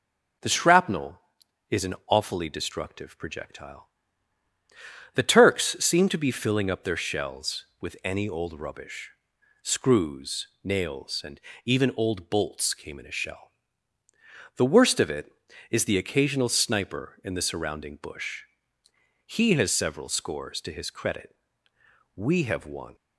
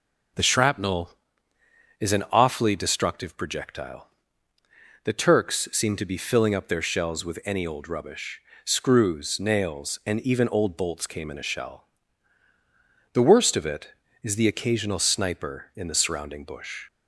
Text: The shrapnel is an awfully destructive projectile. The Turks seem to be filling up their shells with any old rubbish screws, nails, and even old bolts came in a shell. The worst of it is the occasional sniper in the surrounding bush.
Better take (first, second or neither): second